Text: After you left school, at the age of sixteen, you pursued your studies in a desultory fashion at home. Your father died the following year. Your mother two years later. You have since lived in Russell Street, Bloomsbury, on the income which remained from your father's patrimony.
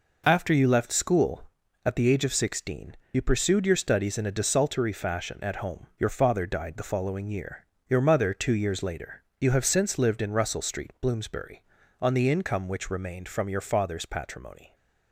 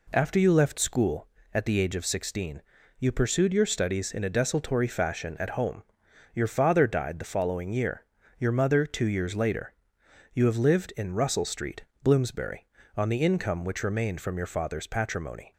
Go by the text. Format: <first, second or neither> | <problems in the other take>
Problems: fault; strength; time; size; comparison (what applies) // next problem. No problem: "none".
first | skips "since"; at 10.5 s